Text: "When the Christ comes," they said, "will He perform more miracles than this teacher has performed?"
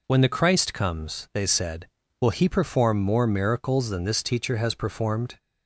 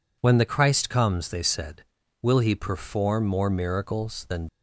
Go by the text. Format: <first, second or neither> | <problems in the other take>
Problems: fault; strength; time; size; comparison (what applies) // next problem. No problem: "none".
first | stops before "this teacher has performed"; at 4.4 s